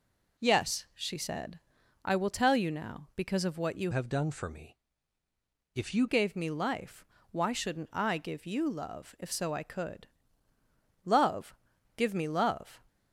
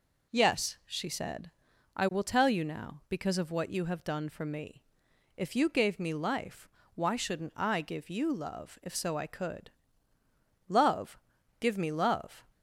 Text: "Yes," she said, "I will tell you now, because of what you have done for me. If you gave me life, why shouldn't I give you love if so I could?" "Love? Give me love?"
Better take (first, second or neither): second